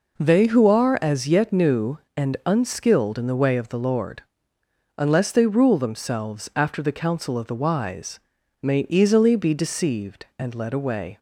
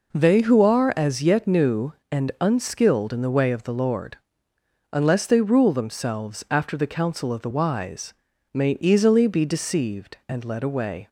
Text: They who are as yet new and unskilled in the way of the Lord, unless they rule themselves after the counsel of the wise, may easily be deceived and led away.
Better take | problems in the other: neither | none

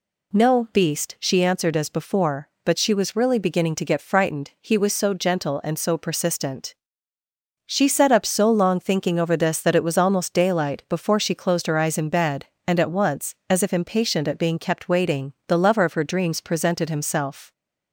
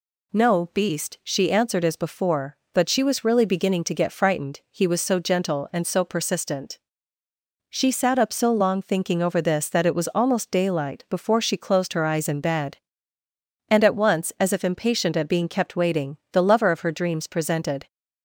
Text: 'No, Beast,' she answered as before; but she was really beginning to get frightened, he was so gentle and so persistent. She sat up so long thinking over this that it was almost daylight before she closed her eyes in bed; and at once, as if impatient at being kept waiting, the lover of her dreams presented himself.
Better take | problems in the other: first | stops before "himself"; at 17.8 s

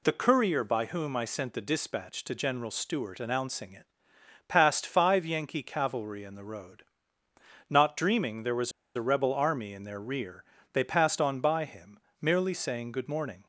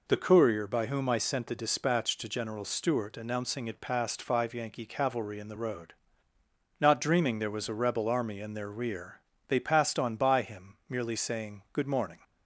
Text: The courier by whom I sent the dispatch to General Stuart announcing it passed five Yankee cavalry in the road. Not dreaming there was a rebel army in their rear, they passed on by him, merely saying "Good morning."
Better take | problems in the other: second | pauses between "it" and "passed"; noticeable; at 3.8 s; 0.64 s long // pauses between "was" and "a"; slight; at 8.6 s; 0.25 s long

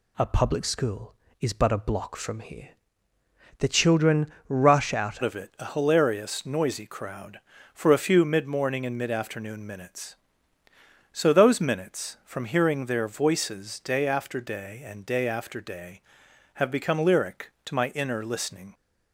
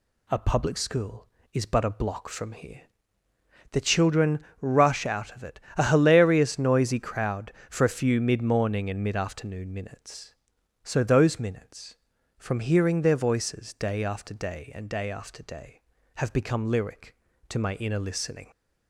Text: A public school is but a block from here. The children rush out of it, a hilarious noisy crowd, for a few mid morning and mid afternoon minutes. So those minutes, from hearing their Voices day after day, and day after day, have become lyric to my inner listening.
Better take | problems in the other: second | pauses between "children" and "rush"; slight; at 4.2 s; 0.20 s long; slight in the second // changes voice at "of"; from 5.2 s on; 13.5 s long

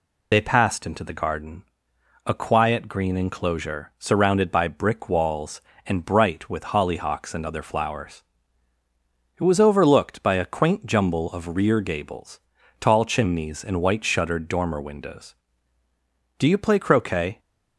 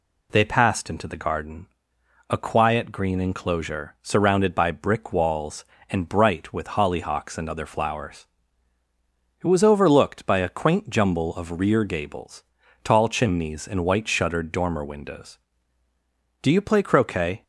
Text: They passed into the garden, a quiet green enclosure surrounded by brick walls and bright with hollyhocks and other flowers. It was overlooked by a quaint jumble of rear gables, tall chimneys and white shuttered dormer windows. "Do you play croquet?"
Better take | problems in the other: second | loses the start of "They"; at 0.3 s; 45 ms

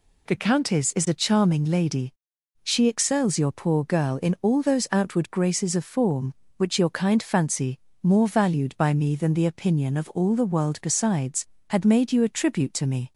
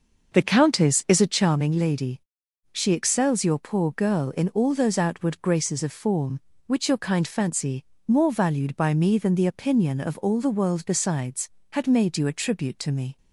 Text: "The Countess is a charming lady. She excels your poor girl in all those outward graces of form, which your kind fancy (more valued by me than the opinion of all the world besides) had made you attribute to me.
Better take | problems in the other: first | starts louder than the rest; noticeable; until 1.6 s; 6 dB

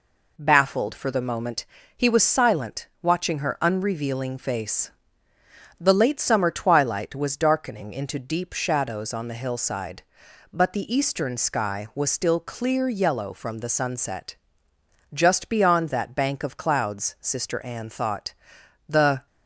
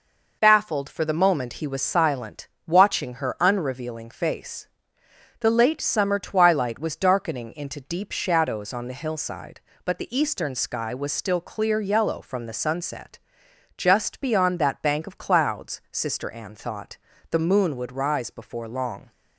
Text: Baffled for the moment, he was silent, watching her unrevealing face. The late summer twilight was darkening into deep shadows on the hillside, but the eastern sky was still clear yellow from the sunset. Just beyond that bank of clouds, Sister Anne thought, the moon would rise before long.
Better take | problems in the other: second | stops before "moon would rise before long"; at 19.2 s

